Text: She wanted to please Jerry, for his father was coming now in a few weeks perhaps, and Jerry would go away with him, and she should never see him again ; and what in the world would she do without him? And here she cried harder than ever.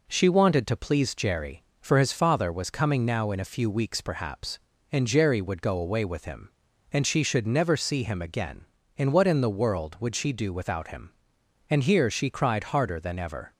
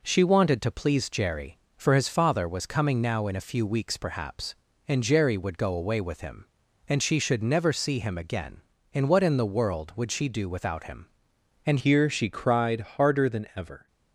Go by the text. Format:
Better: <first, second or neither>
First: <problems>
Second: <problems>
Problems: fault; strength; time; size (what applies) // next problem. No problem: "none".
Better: first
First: none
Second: changes voice at "here"; from 11.7 s on; 2.1 s long